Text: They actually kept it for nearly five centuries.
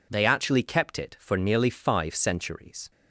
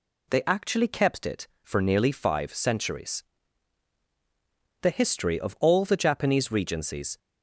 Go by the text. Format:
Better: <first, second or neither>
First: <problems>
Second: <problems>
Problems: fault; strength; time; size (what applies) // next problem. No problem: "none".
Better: first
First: none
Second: goes on to say "The history of all the Japanese regencies"; strong; from 4.8 s on; 2.3 s long